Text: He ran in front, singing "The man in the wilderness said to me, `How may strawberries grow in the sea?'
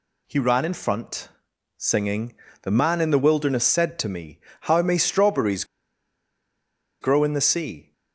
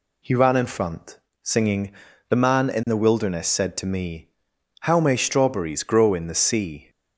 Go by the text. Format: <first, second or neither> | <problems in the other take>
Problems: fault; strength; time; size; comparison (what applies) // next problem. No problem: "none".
second | pauses between "singing" and "The"; slight; at 2.3 s; 0.28 s long; also in the second // pauses between "strawberries" and "grow"; strong; at 5.6 s; 1.3 s long